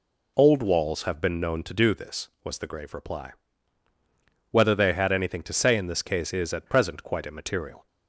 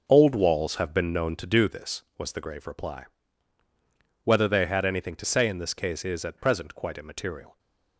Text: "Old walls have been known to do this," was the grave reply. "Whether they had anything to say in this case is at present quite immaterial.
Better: first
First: none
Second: gets quieter; strong; throughout; 10 dB // stays silent after the last word; slight; from 7.4 s on; 0.5 s long

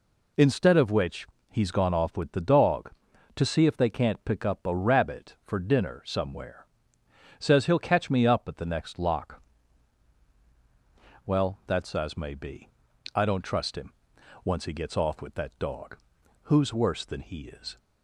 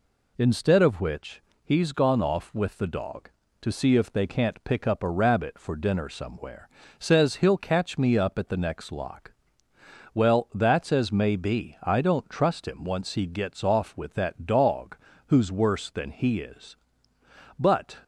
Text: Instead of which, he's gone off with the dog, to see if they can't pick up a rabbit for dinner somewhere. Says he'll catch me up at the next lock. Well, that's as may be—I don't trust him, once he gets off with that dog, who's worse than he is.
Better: first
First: none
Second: goes on to say "But"; slight; from 17.5 s on; 0.38 s long

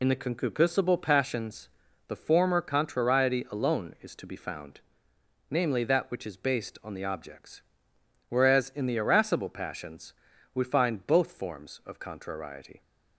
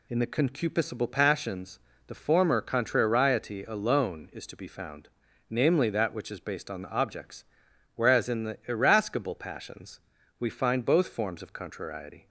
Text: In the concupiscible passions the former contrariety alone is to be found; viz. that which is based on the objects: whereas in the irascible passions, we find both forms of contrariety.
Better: second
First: loses the start of "In"; at 0.0 s; 40 ms // pauses between "passions" and "the"; at 1.6 s; 0.40 s long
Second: pauses between "passions" and "the"; slight; at 1.7 s; 0.30 s long

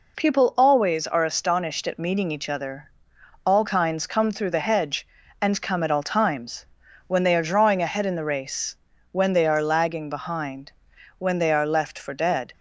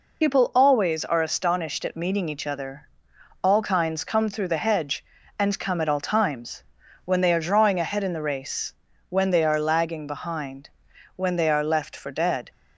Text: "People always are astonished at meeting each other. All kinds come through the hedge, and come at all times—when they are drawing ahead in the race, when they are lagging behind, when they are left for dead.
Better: first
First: none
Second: loses the start of "People"; at 0.2 s; 70 ms

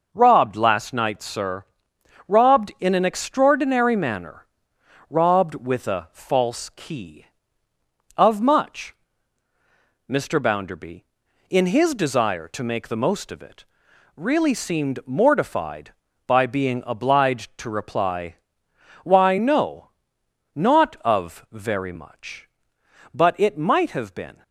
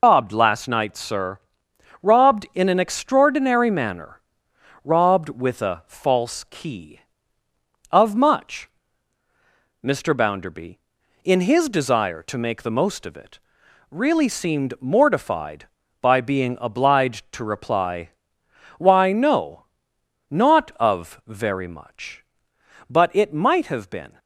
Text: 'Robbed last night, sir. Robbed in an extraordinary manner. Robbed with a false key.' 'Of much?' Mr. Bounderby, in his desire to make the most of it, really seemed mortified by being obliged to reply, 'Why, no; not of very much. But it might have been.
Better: first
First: none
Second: loses the start of "Robbed"; at 0.0 s; 130 ms

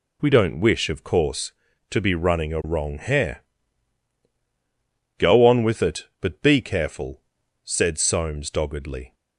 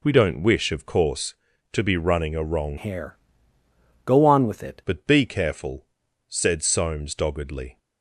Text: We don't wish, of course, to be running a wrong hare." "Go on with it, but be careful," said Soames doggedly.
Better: first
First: none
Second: changes voice from "hare" to "it"; from 2.7 to 4.8 s; 2.1 s long

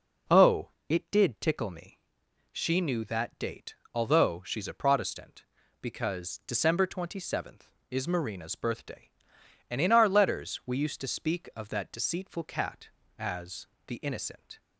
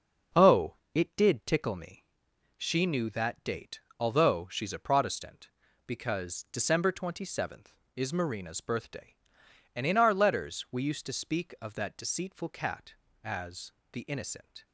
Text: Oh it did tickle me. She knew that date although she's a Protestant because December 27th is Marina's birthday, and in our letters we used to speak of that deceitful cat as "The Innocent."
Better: first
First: pauses between "Oh" and "it"; slight; at 0.6 s; 0.22 s long // pauses between "date" and "although"; slight; at 3.7 s; 0.18 s long // pauses between "as" and "The"; slight; at 13.6 s; 0.18 s long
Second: gets quieter; noticeable; throughout; 6 dB // pauses between "Oh" and "it"; slight; at 0.7 s; 0.22 s long // pauses between "date" and "although"; slight; at 3.8 s; 0.18 s long // pauses between "as" and "The"; slight; at 13.7 s; 0.18 s long

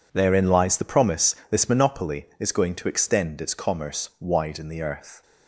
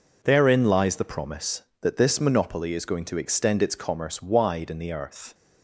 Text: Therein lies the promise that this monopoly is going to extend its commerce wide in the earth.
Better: second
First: skips "that"; at 1.4 s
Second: none

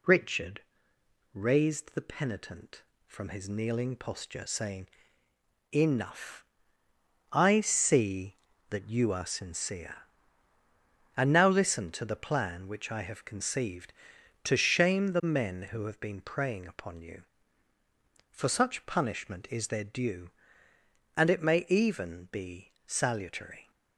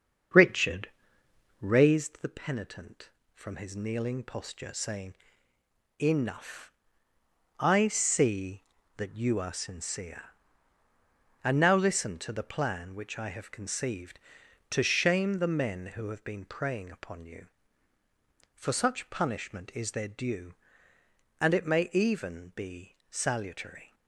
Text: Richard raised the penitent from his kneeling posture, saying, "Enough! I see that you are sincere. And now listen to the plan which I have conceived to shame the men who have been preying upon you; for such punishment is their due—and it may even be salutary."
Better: first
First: pauses between "Richard" and "raised"; noticeable; at 0.6 s; 0.70 s long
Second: starts louder than the rest; until 2.1 s; 7 dB // pauses between "Richard" and "raised"; noticeable; at 0.8 s; 0.70 s long

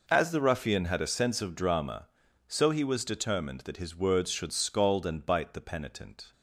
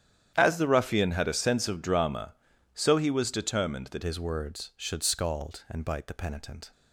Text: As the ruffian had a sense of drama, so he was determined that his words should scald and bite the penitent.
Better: first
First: none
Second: starts louder than the rest; strong; until 1.3 s; 10 dB // changes voice at "his"; from 4.0 s on; 2.7 s long

